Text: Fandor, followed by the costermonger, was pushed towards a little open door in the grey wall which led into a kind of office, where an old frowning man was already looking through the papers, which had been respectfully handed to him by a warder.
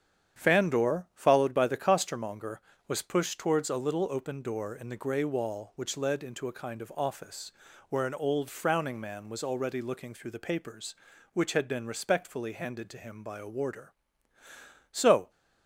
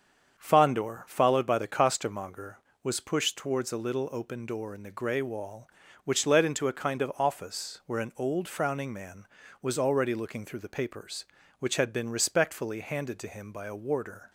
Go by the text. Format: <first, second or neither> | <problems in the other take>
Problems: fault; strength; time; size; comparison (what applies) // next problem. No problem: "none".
second | starts louder than the rest; strong; until 1.4 s; 9 dB; strong in the second // goes on to say "So"; slight; from 14.9 s on; 0.38 s long